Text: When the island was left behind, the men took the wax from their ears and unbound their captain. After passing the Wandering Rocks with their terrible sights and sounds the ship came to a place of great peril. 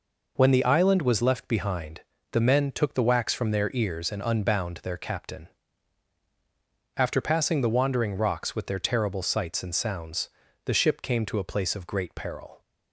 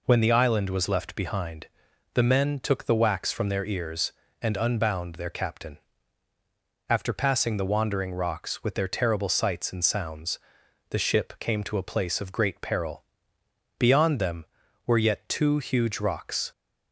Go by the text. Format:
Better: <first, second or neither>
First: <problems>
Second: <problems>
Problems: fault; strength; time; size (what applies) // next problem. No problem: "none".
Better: first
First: pauses between "sounds" and "the"; at 10.2 s; 0.38 s long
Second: pauses between "sounds" and "the"; noticeable; at 10.3 s; 0.50 s long // goes on to say "Beyond them were yet two huge rocks"; strong; from 13.7 s on; 2.7 s long